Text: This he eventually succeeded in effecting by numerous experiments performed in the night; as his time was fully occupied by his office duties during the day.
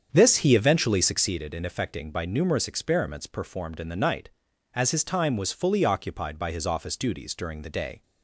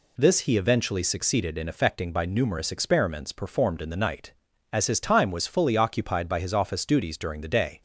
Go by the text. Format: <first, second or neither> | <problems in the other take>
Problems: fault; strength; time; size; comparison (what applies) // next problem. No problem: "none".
second | starts louder than the rest; strong; until 1.4 s; 7.5 dB